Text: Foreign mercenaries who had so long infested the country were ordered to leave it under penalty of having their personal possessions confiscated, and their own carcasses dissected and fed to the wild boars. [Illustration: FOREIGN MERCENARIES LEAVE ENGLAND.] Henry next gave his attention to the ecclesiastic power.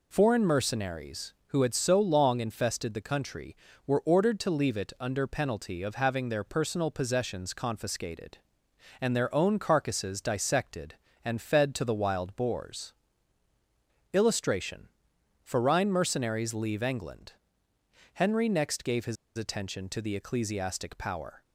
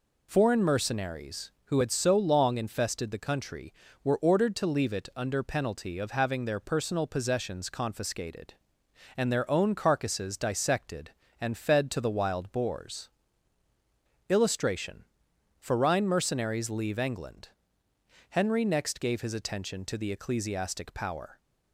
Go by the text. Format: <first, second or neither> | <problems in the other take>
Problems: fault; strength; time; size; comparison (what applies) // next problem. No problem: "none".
second | pauses between "his" and "attention"; slight; at 19.1 s; 0.20 s long